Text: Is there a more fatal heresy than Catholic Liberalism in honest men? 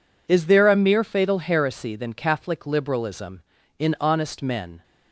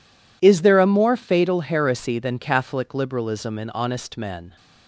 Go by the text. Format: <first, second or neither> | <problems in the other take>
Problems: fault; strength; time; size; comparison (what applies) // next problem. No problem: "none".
second | says "mere" for "more"; at 0.7 s